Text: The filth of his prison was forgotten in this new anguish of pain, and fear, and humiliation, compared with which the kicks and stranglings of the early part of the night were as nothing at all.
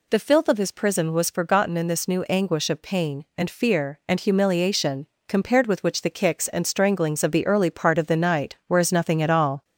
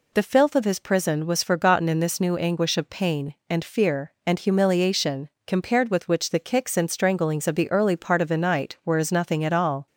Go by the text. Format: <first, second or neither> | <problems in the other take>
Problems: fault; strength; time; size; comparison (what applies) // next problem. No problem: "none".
second | gets louder; slight; throughout; 2.5 dB